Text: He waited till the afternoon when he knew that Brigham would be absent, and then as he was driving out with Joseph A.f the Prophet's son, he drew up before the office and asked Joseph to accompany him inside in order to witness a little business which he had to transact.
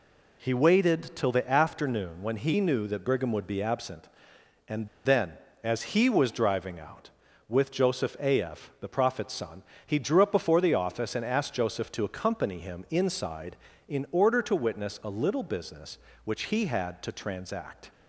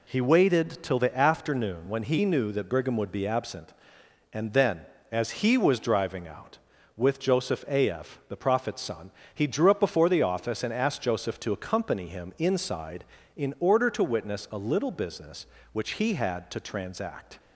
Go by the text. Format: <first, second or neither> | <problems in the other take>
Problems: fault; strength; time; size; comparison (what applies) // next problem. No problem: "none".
second | pauses between "and" and "then"; slight; at 4.8 s; 0.17 s long